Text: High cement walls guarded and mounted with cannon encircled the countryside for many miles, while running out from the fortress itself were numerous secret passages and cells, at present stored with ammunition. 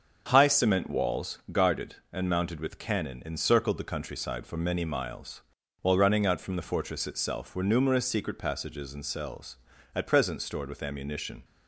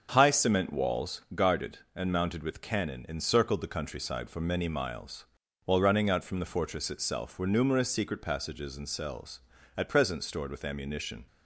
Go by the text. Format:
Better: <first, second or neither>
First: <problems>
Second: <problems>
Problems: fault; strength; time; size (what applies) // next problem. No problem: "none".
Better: neither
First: starts louder than the rest; until 1.2 s; 7 dB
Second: starts louder than the rest; until 1.1 s; 7 dB